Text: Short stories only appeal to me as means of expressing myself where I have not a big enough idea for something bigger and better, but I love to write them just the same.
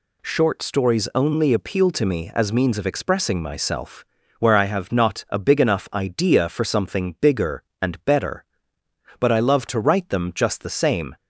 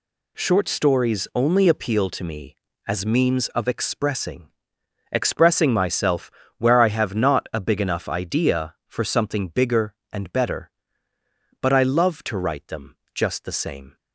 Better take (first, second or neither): first